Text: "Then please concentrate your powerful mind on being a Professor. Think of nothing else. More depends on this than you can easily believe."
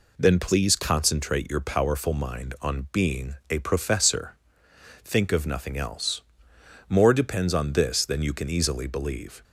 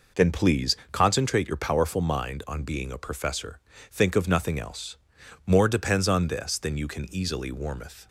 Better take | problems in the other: first | pauses between "please" and "concentrate"; slight; at 0.7 s; 0.16 s long // says "warmeth" for "believe"; at 7.5 s

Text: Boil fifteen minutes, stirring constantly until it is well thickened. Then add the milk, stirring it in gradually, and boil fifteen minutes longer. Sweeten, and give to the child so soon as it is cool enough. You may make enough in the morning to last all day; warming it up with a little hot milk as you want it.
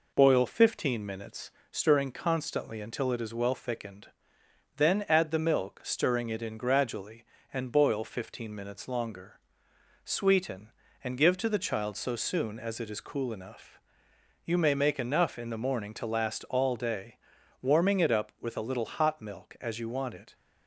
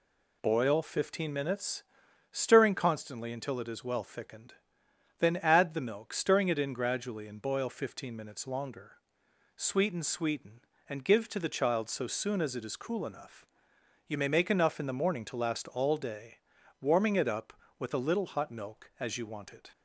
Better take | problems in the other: first | says "Sweeten" twice; at 10.0 s

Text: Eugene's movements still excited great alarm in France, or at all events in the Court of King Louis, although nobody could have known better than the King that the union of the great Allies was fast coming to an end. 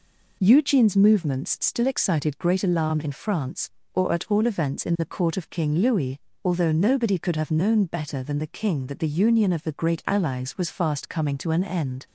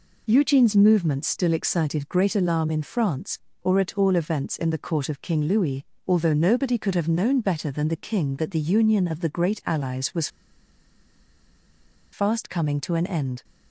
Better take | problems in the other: first | pauses between "was" and "fast"; strong; at 10.2 s; 1.8 s long

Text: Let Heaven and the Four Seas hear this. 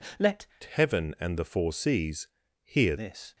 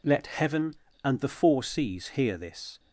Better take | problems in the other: second | changes voice from "Heaven" to "hear"; from 0.6 to 2.9 s; 2.3 s long // pauses between "Seas" and "hear"; slight; at 2.2 s; 0.36 s long

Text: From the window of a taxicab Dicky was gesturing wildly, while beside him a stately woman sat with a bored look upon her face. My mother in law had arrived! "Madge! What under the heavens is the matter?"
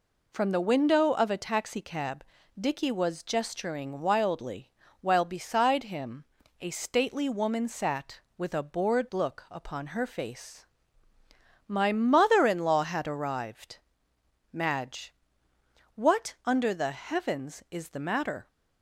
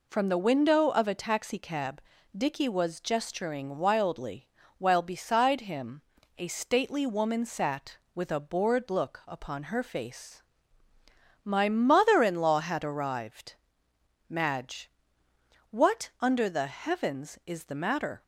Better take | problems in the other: neither | pauses between "taxicab" and "Dicky"; slight; the same in both // pauses between "him" and "a"; the same in both

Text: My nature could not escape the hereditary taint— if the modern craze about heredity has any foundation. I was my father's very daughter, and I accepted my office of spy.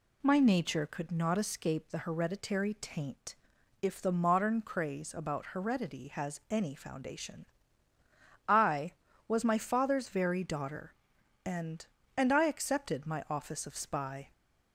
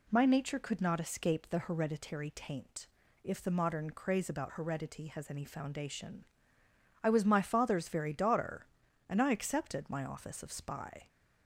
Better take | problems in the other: second | says "and" twice; at 12.1 s

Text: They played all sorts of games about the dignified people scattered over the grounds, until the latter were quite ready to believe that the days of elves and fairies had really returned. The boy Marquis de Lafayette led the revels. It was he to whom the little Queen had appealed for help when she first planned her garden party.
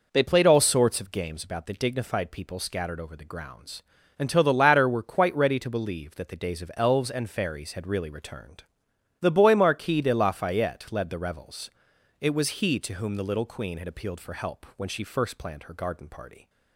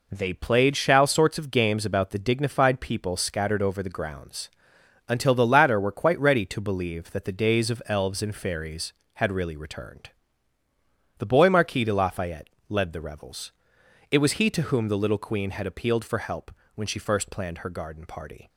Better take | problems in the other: first | says "shall" for "all"; at 0.7 s // pauses between "Lafayette" and "led"; slight; at 12.4 s; 0.20 s long // pauses between "help" and "when"; slight; at 16.5 s; 0.22 s long

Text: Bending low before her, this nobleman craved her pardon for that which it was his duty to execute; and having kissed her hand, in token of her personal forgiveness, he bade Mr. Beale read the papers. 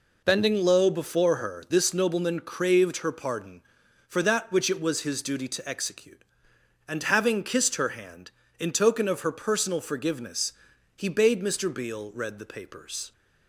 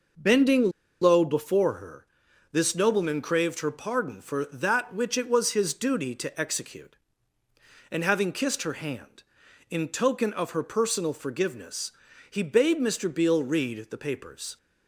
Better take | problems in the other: first | pauses between "Bending" and "low"; slight; at 0.7 s; 0.30 s long

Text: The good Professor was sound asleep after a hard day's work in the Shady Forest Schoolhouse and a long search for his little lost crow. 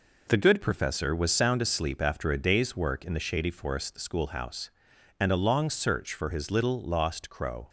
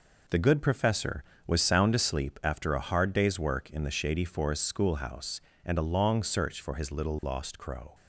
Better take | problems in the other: second | skips "hard"; at 2.3 s

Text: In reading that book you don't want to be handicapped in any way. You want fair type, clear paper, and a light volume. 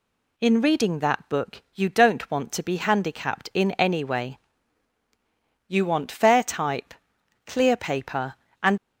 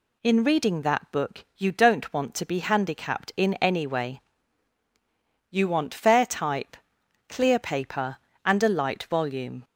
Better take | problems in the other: second | stops before "a light volume"; at 8.7 s

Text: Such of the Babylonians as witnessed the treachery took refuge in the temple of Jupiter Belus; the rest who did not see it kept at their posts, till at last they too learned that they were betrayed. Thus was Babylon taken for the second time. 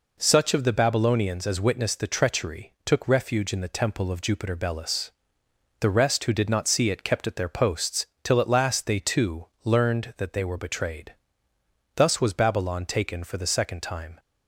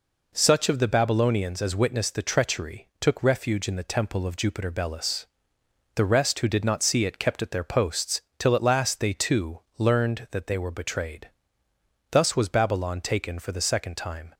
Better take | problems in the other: neither | pauses between "too" and "learned"; slight; the same in both

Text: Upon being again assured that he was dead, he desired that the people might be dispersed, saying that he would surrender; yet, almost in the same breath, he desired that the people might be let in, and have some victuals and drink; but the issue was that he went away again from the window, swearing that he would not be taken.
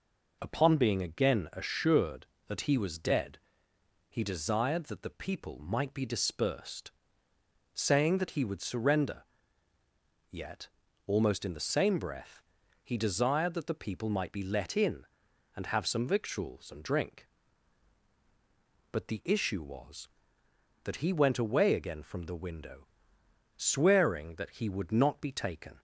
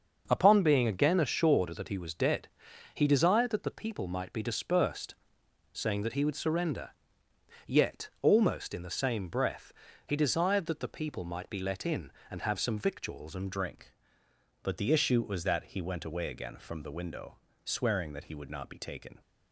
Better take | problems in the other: first | starts louder than the rest; until 1.2 s; 6.5 dB // changes voice at "drink"; from 13.5 s on; 5.6 s long

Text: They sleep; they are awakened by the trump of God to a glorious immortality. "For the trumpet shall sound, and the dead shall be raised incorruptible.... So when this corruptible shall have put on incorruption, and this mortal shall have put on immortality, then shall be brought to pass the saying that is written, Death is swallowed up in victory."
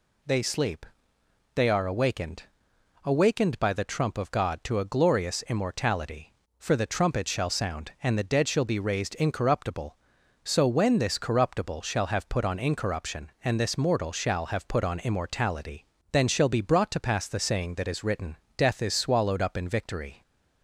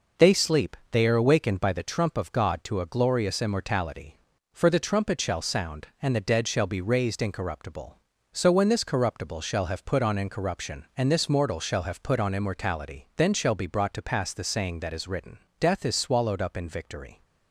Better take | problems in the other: second | says "awakened" twice; at 3.0 s

